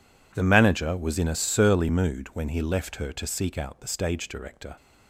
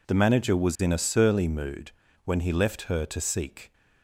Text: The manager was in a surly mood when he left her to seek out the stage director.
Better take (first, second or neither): first